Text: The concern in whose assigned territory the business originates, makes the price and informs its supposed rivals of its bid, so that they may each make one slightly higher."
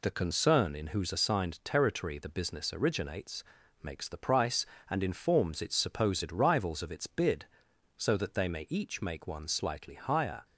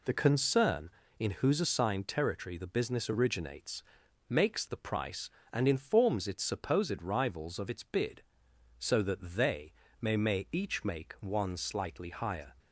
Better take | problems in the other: first | pauses between "they" and "may"; slight; at 9.7 s; 0.28 s long // says "may" twice; at 10.1 s

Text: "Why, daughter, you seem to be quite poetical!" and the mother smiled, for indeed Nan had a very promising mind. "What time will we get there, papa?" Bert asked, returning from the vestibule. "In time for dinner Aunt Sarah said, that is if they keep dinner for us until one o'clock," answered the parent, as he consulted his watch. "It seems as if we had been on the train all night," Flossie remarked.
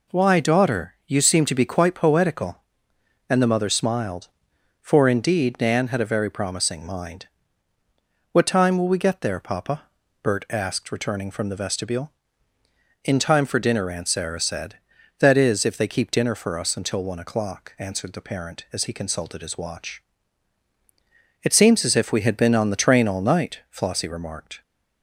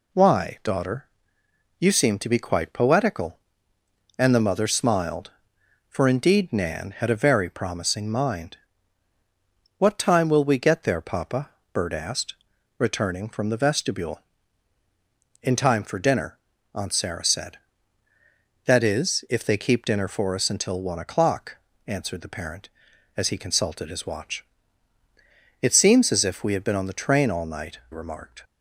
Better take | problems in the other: first | pauses between "dinner" and "Aunt"; slight; at 16.3 s; 0.36 s long // skips "Flossie"; at 27.8 s

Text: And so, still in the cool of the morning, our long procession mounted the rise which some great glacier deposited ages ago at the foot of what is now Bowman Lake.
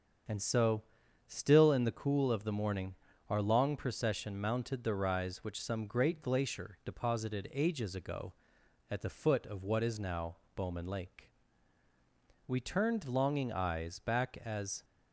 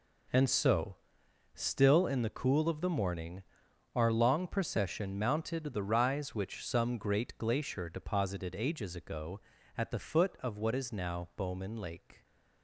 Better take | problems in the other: second | starts louder than the rest; strong; until 1.7 s; 7 dB // pauses between "now" and "Bowman"; slight; at 10.3 s; 0.20 s long // goes on to say "We turned longing eyes back as"; strong; from 12.4 s on; 2.3 s long

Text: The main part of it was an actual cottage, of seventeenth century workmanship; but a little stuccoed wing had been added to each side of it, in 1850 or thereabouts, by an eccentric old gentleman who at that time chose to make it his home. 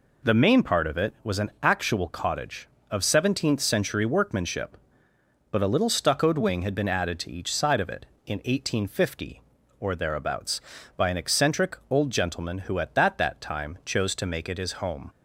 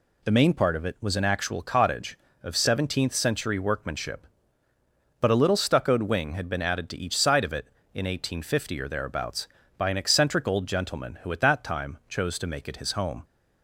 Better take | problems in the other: second | says "that" twice; at 13.1 s

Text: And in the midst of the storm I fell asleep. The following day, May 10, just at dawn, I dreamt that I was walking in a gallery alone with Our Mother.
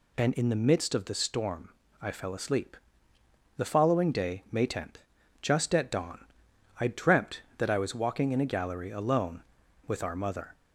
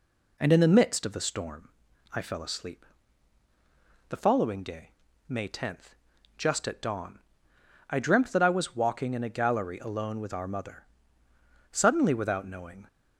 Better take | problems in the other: first | pauses between "storm" and "I"; at 1.6 s; 0.44 s long; slight in the first // goes on to say "Suddenly without knowing"; noticeable; from 11.7 s on; 1.1 s long

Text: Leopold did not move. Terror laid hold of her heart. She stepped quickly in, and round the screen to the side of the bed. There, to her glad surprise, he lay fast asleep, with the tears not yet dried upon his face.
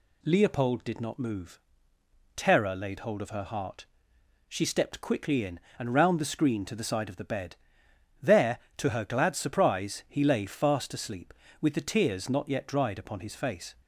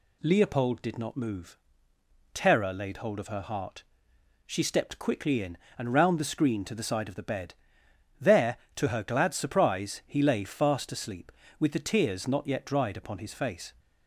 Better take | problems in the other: neither | none

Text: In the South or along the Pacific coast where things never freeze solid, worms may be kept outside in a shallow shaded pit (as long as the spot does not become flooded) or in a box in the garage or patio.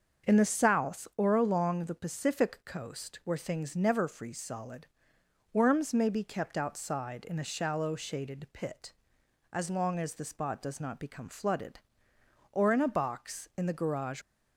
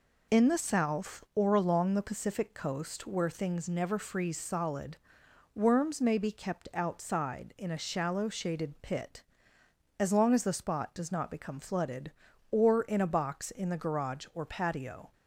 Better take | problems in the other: second | starts louder than the rest; until 1.3 s; 6.5 dB // stops before "or patio"; at 14.2 s

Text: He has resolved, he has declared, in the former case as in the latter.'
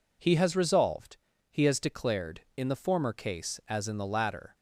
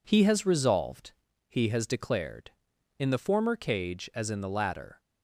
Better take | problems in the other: first | says "cage" for "case"; at 3.5 s

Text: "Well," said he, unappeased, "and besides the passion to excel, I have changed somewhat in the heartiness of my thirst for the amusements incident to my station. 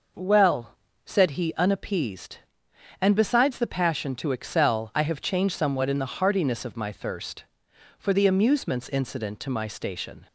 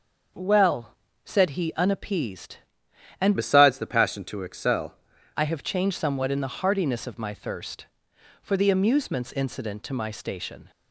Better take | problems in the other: first | starts louder than the rest; noticeable; until 1.6 s; 6 dB // changes voice from "besides" to "excel"; from 3.3 to 4.9 s; 1.6 s long

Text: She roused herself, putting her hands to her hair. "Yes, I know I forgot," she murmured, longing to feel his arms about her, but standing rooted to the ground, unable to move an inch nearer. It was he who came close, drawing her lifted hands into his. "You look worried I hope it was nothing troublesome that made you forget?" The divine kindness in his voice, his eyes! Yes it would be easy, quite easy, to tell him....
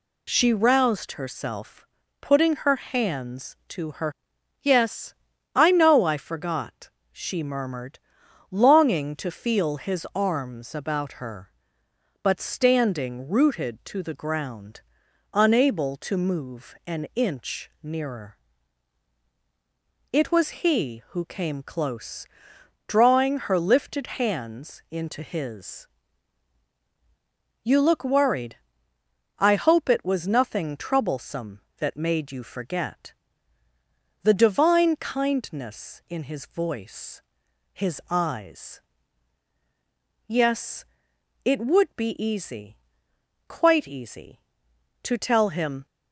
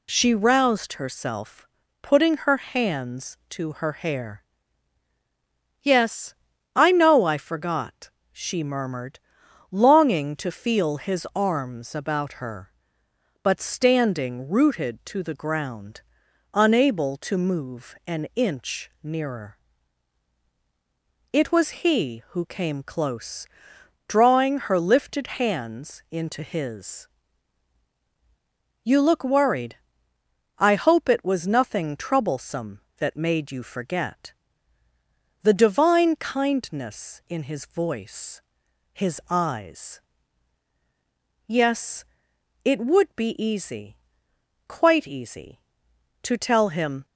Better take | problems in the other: second | skips "hair"; at 4.3 s // pauses between "worried" and "I"; noticeable; at 28.5 s; 0.84 s long; noticeable in the second // pauses between "Yes" and "it"; noticeable; at 40.8 s; 0.62 s long; noticeable in the second

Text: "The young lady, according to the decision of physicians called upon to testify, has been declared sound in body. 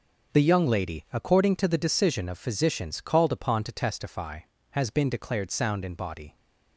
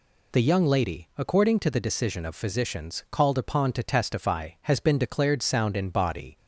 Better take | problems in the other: neither | none

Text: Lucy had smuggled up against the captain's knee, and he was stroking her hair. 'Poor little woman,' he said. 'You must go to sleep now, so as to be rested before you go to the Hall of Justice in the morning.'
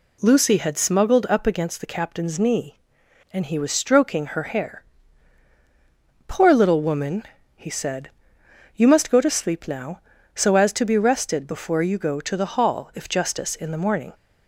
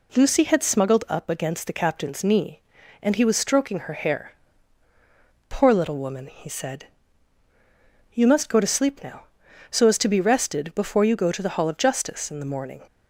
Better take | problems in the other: second | says "if" for "of"; at 12.9 s

